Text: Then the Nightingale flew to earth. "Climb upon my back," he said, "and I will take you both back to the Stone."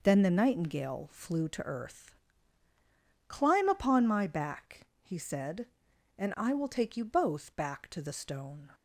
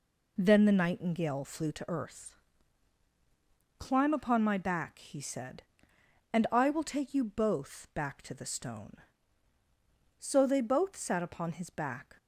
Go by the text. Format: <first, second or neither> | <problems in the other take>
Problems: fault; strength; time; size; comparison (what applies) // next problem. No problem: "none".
first | goes on to say "So they both sat upon his back"; strong; from 10.1 s on; 1.9 s long